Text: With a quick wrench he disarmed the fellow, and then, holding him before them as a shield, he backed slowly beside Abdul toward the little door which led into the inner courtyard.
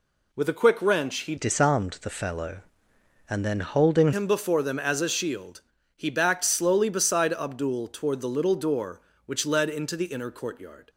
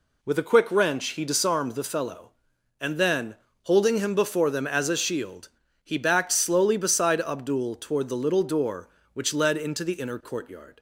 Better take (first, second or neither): second